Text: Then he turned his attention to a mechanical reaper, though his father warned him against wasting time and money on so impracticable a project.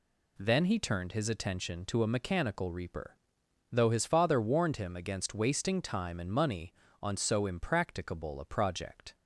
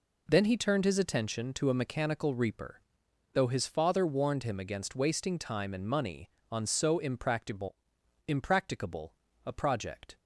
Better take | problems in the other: first | says "impracticable" twice; at 8.2 s

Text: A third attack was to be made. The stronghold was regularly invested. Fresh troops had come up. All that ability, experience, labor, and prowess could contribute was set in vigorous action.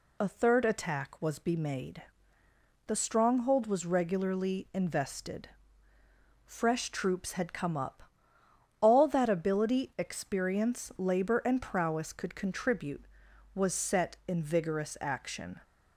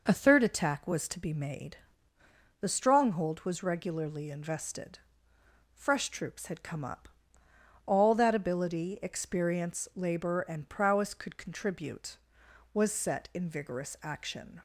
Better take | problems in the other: second | skips "to"; at 1.4 s

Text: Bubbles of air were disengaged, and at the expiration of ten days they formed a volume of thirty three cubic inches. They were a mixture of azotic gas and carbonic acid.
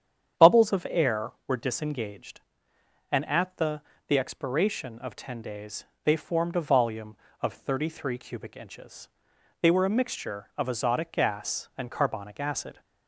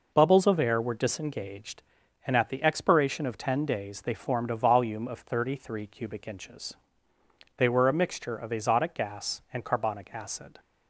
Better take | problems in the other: second | starts louder than the rest; strong; until 1.6 s; 9 dB // says "the" twice; at 4.0 s // pauses between "days" and "they"; slight; at 5.8 s; 0.18 s long

